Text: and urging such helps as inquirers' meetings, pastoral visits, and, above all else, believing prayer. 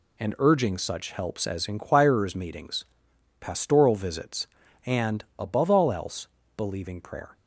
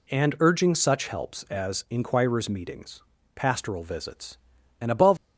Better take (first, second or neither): first